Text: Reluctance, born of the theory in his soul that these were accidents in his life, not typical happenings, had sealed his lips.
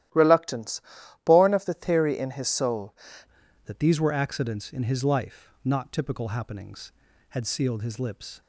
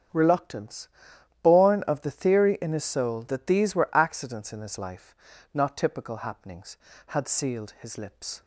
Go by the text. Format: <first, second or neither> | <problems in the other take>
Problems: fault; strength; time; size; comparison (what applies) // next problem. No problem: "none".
second | starts louder than the rest; strong; until 1.5 s; 13.5 dB; strong in the second // changes voice at "that"; from 3.6 s on; 4.8 s long